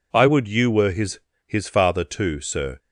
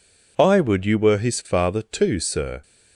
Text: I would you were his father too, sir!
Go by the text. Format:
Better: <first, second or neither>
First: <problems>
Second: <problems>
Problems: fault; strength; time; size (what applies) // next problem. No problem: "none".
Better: second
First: says "his" twice; at 1.4 s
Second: none